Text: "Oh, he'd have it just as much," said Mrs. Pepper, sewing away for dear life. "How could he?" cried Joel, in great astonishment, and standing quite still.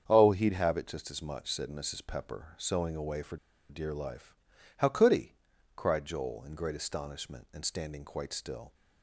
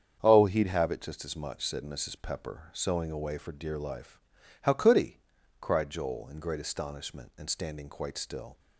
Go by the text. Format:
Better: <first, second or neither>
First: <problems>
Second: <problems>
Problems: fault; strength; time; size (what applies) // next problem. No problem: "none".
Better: second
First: starts louder than the rest; strong; until 1.0 s; 7.5 dB // pauses between "for" and "dear"; slight; at 3.3 s; 0.32 s long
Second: starts louder than the rest; strong; until 1.2 s; 7.5 dB